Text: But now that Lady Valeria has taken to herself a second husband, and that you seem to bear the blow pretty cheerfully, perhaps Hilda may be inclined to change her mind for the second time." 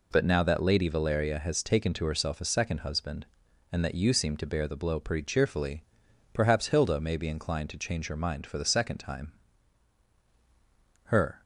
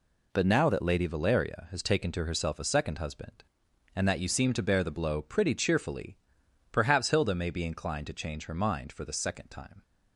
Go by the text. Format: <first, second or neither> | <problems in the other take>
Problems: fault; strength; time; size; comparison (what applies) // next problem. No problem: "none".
second | goes on to say "Her"; slight; from 11.0 s on; 0.38 s long